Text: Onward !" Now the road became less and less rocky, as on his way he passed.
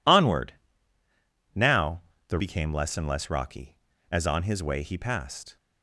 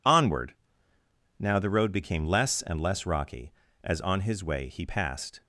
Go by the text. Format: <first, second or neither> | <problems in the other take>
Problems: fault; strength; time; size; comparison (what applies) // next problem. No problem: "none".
second | pauses between "Now" and "the"; slight; at 2.0 s; 0.26 s long // skips "road"; at 2.3 s